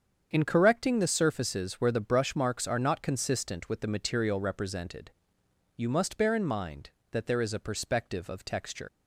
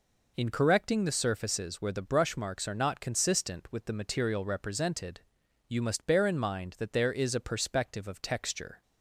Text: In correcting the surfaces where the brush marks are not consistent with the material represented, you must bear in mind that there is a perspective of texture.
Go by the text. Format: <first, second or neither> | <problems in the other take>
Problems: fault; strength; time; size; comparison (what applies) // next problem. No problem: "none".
second | starts louder than the rest; strong; until 1.3 s; 7.5 dB // leaves "texture" unfinished; at 8.8 s; 85 ms